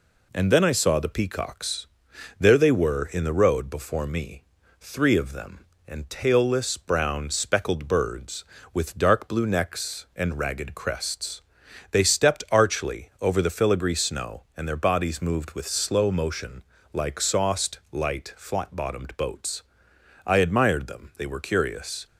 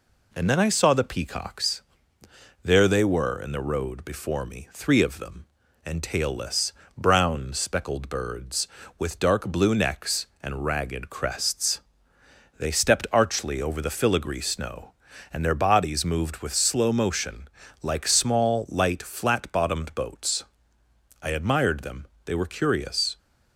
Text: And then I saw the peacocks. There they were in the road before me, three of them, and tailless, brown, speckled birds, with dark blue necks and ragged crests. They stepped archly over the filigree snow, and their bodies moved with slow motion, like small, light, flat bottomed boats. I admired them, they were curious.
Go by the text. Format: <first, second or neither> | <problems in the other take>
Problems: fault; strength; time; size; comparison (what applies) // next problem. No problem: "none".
second | says "sauced" for "small"; at 17.1 s